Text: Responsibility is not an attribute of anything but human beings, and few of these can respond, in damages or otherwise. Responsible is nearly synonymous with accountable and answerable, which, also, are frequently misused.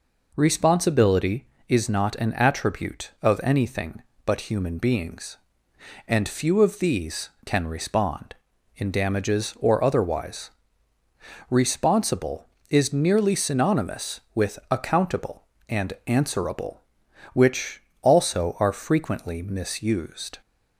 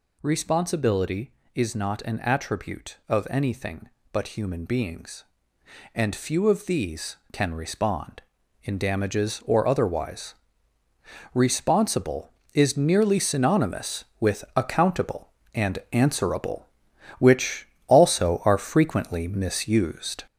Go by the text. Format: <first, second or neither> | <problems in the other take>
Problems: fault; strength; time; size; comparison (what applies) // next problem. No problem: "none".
first | gets louder; noticeable; throughout; 5 dB